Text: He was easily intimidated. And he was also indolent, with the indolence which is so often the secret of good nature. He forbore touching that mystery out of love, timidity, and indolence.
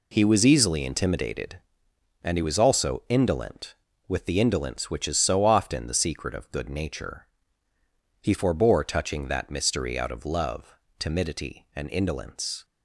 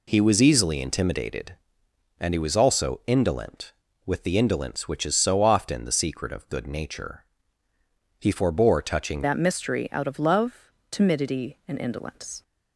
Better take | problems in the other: first | changes voice at "that"; from 9.2 s on; 3.2 s long

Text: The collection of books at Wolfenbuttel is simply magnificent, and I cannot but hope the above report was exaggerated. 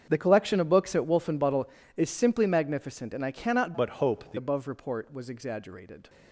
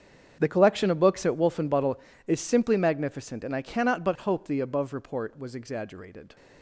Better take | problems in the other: second | starts louder than the rest; strong; until 1.0 s; 7.5 dB; strong in the second // changes voice from "but" to "the"; from 3.7 to 4.3 s; 0.6 s long

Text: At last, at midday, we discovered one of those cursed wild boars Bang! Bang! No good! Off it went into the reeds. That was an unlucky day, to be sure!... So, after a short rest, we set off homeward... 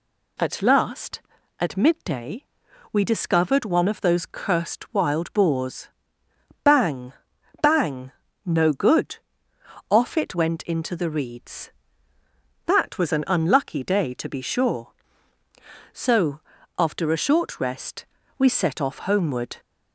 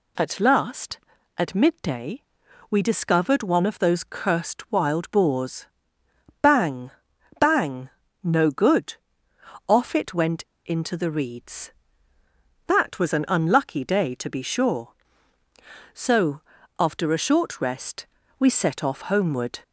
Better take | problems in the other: first | pauses between "boars" and "Bang"; noticeable; at 5.6 s; 0.76 s long; noticeable in the first // pauses between "went" and "into"; slight; at 10.4 s; 0.24 s long

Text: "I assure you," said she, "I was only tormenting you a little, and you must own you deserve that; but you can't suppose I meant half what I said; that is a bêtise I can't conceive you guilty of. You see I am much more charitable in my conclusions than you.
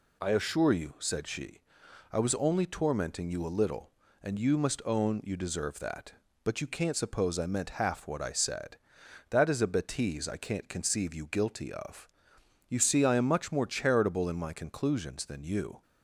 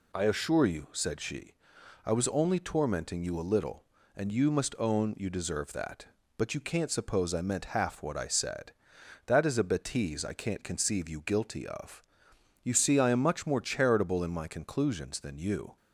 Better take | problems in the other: neither | none

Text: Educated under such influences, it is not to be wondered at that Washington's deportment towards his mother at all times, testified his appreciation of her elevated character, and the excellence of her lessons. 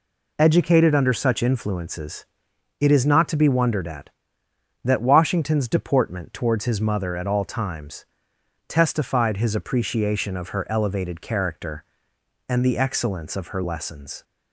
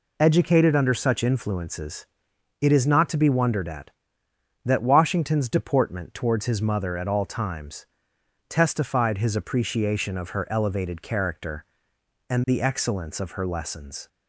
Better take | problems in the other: neither | none

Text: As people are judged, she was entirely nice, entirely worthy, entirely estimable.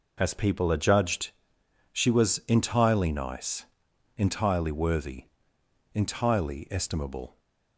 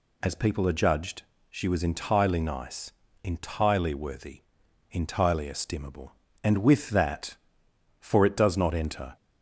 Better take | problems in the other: first | goes on to say "And with that for it does not enter"; strong; from 6.4 s on; 2.7 s long

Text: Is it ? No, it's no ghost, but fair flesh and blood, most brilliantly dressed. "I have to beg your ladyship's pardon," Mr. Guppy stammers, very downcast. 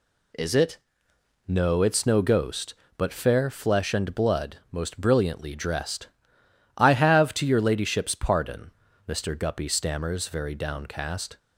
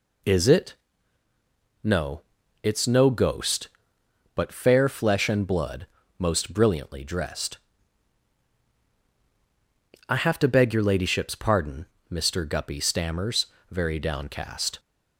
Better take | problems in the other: second | skips "beg"; at 7.4 s

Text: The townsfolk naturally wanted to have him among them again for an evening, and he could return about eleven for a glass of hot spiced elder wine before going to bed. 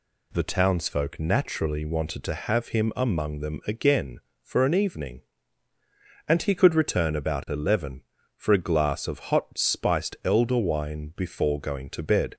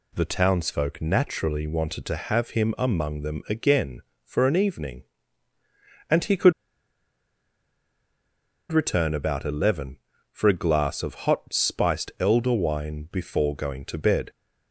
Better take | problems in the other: first | pauses between "could" and "return"; strong; at 6.5 s; 2.1 s long

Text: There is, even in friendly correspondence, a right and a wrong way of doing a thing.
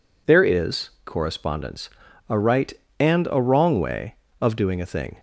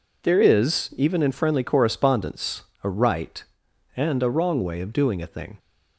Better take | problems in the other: second | skips "even in friendly"; at 0.9 s

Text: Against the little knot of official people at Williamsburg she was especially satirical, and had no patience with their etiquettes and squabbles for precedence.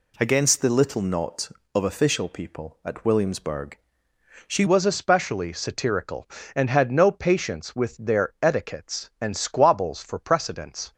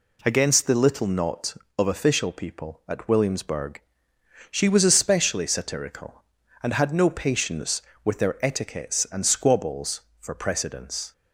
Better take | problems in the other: second | pauses between "Williamsburg" and "she"; noticeable; at 3.7 s; 0.70 s long; noticeable in the second // changes voice at "was"; from 4.6 s on; 6.3 s long

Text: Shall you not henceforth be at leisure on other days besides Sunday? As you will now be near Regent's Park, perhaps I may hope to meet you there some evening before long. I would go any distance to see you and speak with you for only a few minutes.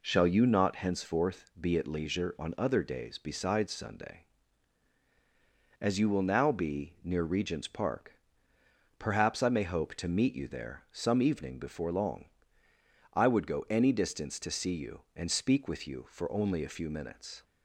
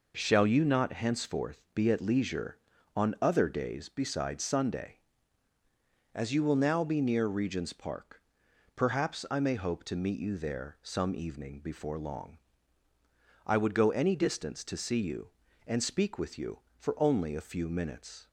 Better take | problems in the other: neither | none

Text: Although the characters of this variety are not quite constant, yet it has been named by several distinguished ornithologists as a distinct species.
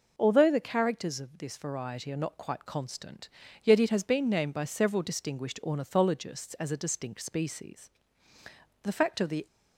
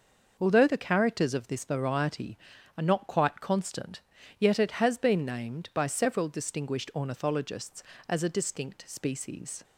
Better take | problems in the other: second | goes on to say "The fact of the"; noticeable; from 8.8 s on; 0.64 s long

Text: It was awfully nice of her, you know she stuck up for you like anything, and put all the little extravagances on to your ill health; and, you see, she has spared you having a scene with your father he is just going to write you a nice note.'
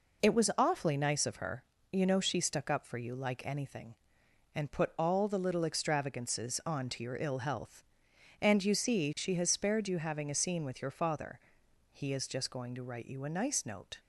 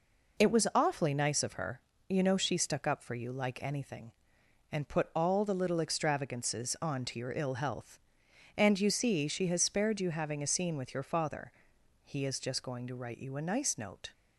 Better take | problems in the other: neither | pauses between "father" and "he"; noticeable; the same in both

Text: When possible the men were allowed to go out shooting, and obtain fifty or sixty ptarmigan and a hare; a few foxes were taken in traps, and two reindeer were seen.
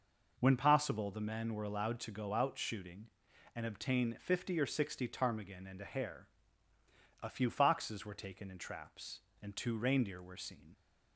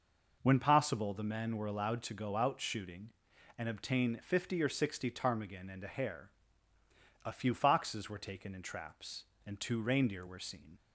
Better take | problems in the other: neither | none

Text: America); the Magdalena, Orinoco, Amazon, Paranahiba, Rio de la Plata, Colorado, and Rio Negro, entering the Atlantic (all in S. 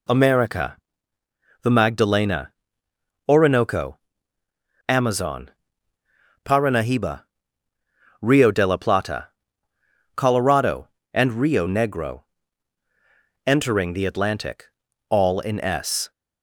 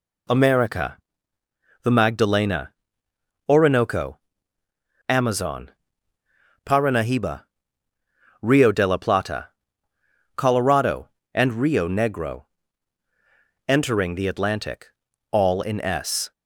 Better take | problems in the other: neither | none

